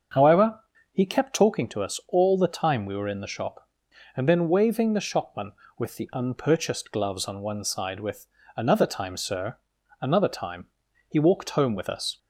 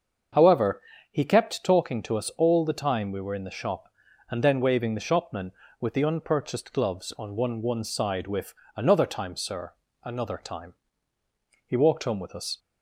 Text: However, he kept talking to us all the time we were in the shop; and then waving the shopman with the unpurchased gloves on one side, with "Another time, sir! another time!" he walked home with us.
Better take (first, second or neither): first